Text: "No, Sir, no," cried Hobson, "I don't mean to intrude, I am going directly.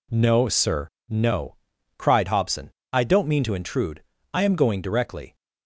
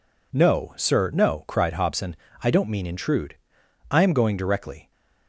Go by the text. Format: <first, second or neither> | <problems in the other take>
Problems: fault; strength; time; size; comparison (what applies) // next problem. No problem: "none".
first | skips "to"; at 2.8 s